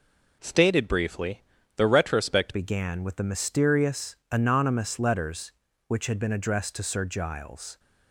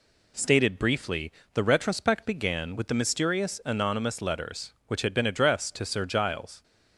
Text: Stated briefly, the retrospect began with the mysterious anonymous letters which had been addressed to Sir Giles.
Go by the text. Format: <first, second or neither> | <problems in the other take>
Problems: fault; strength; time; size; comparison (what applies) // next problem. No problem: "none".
second | changes voice at "began"; from 2.5 s on; 5.2 s long